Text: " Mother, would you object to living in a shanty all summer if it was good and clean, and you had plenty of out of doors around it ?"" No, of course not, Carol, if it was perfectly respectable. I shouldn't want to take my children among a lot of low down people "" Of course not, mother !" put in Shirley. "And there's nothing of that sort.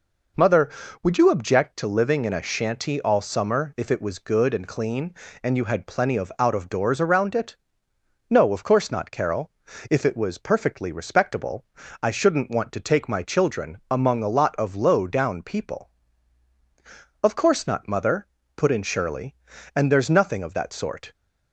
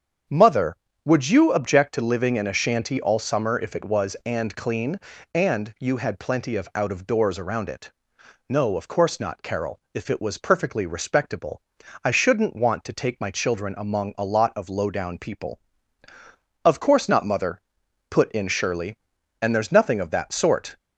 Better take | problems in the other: first | starts louder than the rest; strong; until 1.5 s; 8 dB // skips "good"; at 4.2 s

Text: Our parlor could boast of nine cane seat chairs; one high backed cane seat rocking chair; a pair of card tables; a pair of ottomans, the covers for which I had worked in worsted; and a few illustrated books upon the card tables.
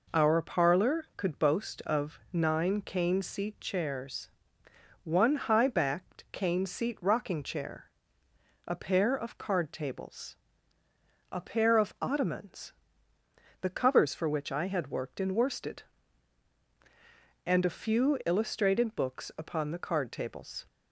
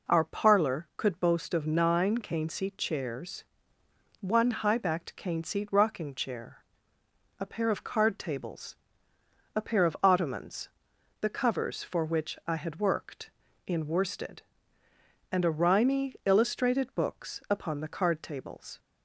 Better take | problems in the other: first | says "rimy" for "few"; at 15.5 s

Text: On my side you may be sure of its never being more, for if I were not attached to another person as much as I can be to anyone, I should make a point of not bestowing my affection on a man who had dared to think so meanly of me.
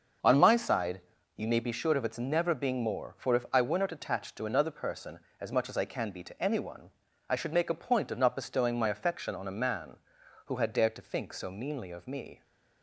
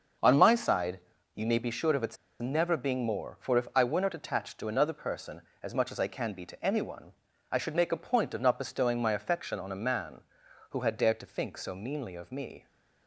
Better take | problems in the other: first | starts louder than the rest; until 1.5 s; 6.5 dB; also in the first // pauses between "side" and "you"; slight; at 0.9 s; 0.36 s long; slight in the first // pauses between "its" and "never"; slight; at 2.1 s; 0.24 s long

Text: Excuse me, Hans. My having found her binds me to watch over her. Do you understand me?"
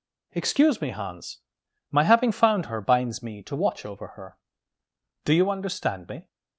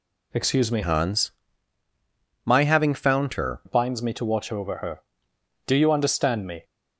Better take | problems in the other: first | changes voice from "Hans" to "her"; from 0.8 to 3.5 s; 2.7 s long

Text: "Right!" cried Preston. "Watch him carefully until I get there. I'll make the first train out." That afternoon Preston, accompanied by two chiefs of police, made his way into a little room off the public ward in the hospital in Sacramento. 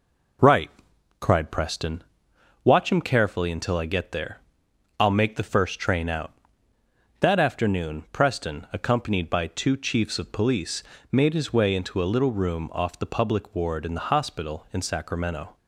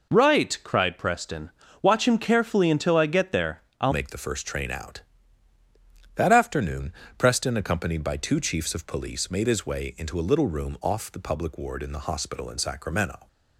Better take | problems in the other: first | changes voice at "make"; from 3.9 s on; 9.3 s long // pauses between "afternoon" and "Preston"; slight; at 6.9 s; 0.26 s long

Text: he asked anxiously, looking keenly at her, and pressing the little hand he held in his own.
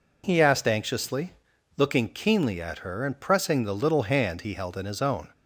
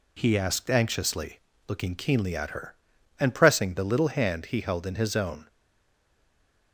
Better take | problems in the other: first | stays silent after the last word; noticeable; from 5.4 s on; 1.3 s long

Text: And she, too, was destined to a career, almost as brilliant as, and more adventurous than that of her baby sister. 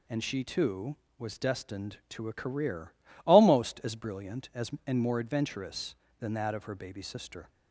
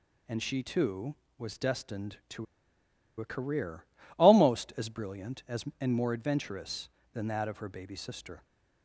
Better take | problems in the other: first | pauses between "to" and "a"; noticeable; at 2.4 s; 0.75 s long

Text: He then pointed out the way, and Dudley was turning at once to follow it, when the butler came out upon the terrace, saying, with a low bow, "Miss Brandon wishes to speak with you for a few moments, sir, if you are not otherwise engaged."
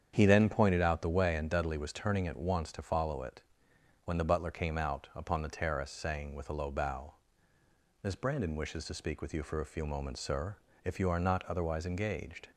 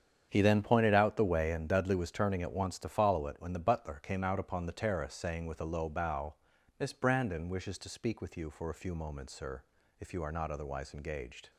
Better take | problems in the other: neither | starts louder than the rest; strong; the same in both

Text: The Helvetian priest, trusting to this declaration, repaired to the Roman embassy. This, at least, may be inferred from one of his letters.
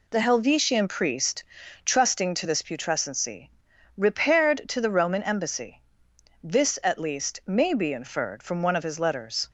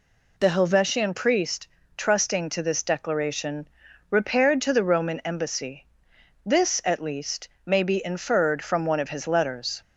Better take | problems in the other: second | says "putrescency" for "declaration"; at 2.6 s

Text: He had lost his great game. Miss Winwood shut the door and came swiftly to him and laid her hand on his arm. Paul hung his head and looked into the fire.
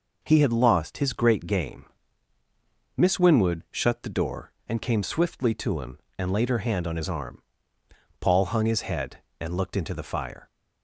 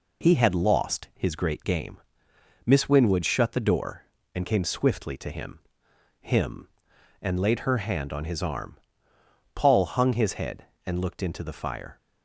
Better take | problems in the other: first | says "him" twice; at 6.1 s

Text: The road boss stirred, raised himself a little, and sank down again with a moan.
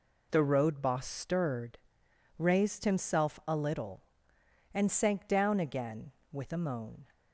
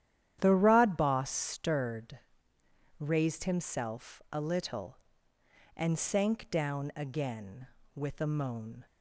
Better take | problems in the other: first | starts louder than the rest; strong; until 1.4 s; 10.5 dB // says "rod" for "road"; at 0.5 s

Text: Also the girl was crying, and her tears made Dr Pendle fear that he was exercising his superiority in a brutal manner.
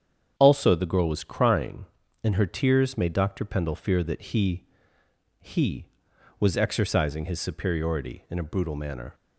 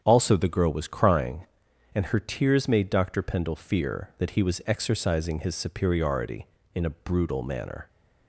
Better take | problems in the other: second | starts louder than the rest; strong; until 1.3 s; 8 dB; strong in the second // says "he" twice; at 5.4 s

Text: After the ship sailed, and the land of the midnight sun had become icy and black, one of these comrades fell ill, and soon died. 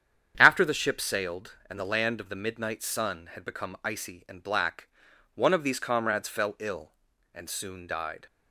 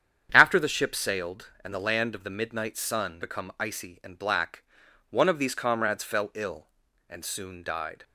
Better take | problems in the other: first | starts louder than the rest; strong; until 1.3 s; 8.5 dB; strong in the first // skips "had"; at 3.2 s

